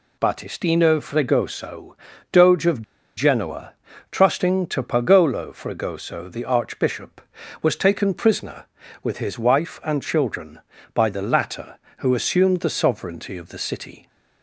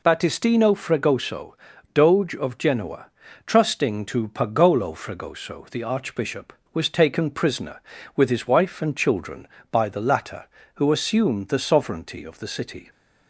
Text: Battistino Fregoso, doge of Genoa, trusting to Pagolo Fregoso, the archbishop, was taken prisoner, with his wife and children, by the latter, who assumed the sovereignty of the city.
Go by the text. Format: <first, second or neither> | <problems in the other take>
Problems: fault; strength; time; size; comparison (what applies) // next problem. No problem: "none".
second | pauses between "of" and "Genoa"; slight; at 2.8 s; 0.35 s long